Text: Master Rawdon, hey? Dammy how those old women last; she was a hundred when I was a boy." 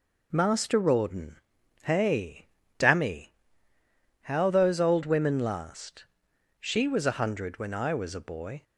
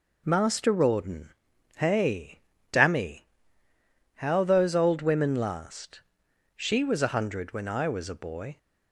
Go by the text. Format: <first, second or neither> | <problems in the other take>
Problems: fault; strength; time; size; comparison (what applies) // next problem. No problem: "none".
neither | pauses between "Dammy" and "how"; noticeable; the same in both